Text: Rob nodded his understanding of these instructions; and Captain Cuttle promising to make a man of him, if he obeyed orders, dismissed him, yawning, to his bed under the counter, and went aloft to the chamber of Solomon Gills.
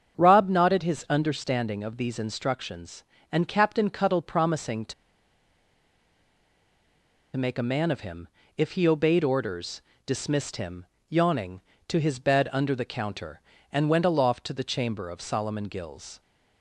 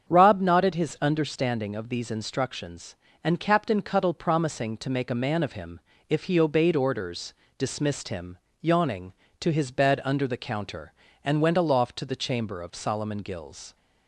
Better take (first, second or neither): second